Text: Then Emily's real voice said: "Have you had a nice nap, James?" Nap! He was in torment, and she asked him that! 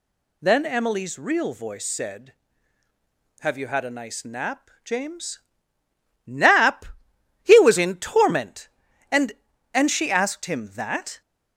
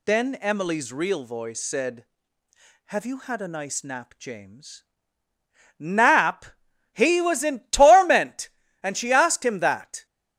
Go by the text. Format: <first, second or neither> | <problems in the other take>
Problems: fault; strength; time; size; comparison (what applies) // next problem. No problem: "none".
second | says "and" twice; at 9.7 s